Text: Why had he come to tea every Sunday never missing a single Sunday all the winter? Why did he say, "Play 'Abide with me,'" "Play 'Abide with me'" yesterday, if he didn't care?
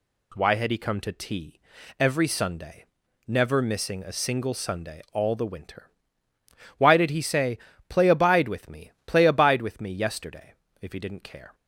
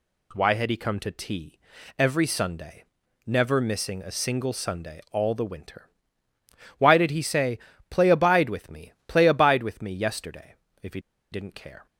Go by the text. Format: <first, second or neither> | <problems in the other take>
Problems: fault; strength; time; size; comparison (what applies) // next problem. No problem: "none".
first | pauses between "tea" and "every"; at 1.5 s; 0.40 s long; also in the first // pauses between "Sunday" and "never"; at 2.8 s; 0.42 s long; also in the first // pauses between "he" and "didn't"; slight; at 10.9 s; 0.32 s long